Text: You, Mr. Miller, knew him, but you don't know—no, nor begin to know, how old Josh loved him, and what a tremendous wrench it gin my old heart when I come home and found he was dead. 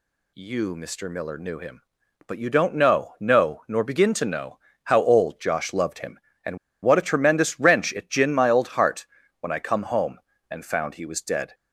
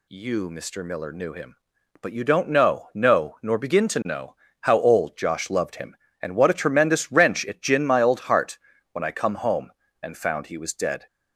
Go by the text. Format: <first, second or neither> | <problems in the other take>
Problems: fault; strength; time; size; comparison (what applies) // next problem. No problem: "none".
second | pauses between "and" and "what"; slight; at 6.5 s; 0.25 s long // pauses between "heart" and "when"; slight; at 9.0 s; 0.32 s long; slight in the second